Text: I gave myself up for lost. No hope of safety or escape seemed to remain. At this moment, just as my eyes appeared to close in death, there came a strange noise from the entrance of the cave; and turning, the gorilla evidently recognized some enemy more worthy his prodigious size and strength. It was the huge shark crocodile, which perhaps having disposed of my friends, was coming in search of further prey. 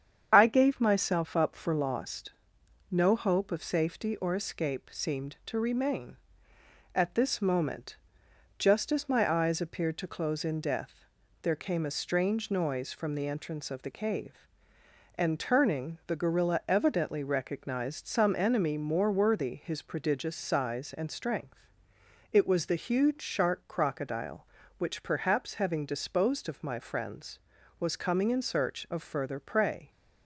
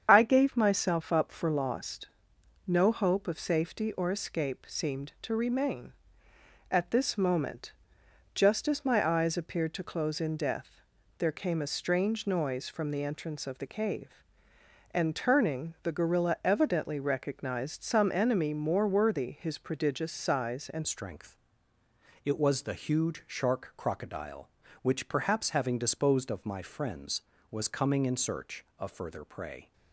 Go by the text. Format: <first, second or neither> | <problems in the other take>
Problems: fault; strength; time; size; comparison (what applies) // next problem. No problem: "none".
first | starts louder than the rest; until 1.1 s; 7 dB; also in the first // changes voice at "strength"; from 20.8 s on; 8.9 s long